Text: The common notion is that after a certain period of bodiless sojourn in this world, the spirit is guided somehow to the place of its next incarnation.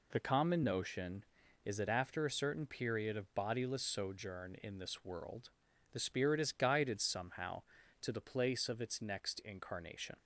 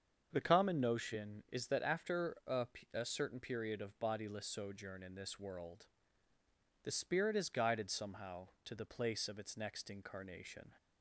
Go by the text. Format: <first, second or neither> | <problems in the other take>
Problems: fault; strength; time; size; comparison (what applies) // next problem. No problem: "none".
first | starts louder than the rest; strong; until 1.3 s; 7 dB // says "a" twice; at 2.9 s